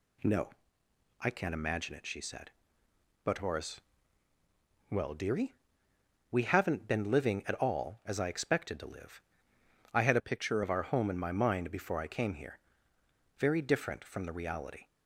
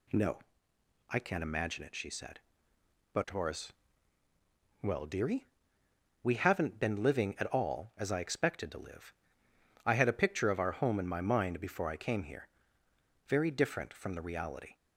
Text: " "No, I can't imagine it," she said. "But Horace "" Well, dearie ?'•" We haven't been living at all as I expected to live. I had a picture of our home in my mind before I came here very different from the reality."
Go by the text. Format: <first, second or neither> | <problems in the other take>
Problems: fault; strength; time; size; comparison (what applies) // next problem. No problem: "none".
second | changes voice from "a" to "picture"; from 10.1 to 10.6 s; 0.5 s long // pauses between "here" and "very"; noticeable; at 12.6 s; 0.78 s long; noticeable in the second